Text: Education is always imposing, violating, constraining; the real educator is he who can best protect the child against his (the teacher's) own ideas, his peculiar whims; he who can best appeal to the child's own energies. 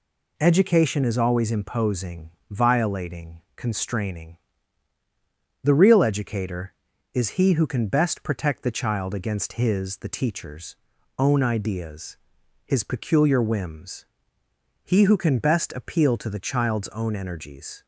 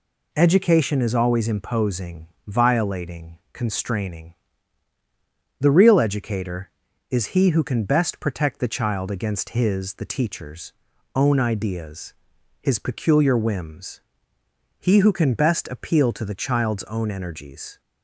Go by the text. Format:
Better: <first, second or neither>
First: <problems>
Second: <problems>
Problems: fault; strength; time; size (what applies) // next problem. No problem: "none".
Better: neither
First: none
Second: none